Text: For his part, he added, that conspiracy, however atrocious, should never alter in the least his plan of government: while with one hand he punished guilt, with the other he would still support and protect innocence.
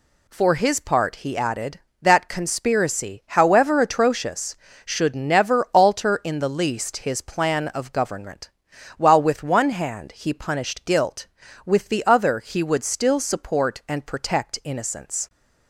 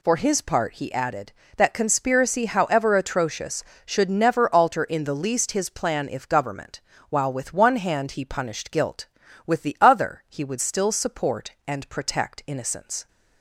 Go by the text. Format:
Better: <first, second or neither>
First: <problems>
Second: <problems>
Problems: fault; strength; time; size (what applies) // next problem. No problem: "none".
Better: first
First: none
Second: says "if" for "of"; at 6.0 s